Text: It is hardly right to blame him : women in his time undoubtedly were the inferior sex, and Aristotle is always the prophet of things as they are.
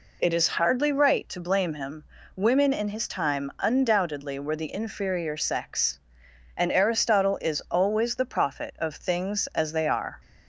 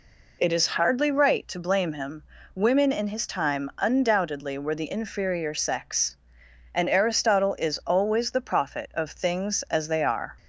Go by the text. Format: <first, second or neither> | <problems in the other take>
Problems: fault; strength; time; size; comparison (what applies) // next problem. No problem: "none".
neither | none